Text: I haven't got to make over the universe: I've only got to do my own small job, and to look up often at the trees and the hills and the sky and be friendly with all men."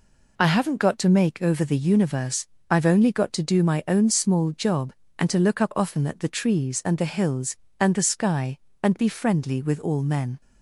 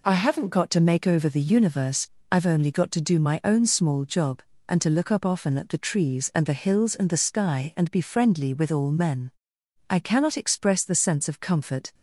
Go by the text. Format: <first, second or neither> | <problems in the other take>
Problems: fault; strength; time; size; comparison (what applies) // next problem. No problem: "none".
first | goes on to say "I cannot express the sense of comfort"; strong; from 9.8 s on; 2.0 s long